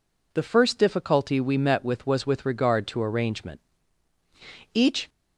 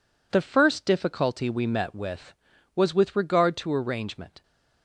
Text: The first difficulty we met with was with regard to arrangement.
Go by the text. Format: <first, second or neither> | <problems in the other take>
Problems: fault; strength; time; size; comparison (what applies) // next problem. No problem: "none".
second | goes on to say "Each"; slight; from 4.7 s on; 0.36 s long